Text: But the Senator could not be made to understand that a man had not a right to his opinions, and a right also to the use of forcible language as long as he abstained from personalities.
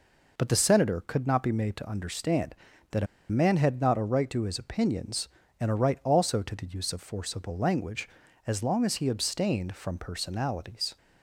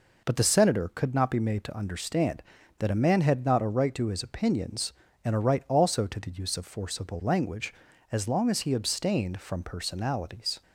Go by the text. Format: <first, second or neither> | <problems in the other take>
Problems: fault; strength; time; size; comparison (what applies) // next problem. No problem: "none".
second | pauses between "a" and "man"; slight; at 3.0 s; 0.24 s long